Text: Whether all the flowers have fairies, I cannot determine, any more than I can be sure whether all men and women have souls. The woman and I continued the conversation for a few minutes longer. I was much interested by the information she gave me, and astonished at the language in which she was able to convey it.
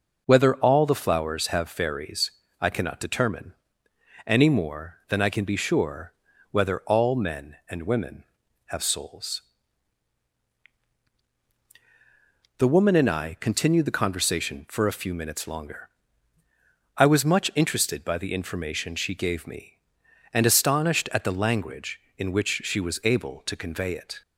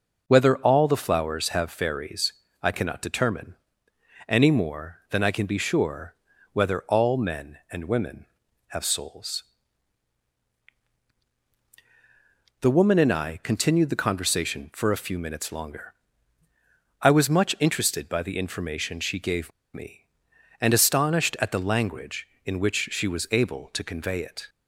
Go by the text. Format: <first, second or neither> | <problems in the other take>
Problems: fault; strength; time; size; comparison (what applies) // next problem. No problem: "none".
first | pauses between "sure" and "whether"; slight; at 6.1 s; 0.36 s long; slight in the first // pauses between "gave" and "me"; slight; at 19.5 s; 0.24 s long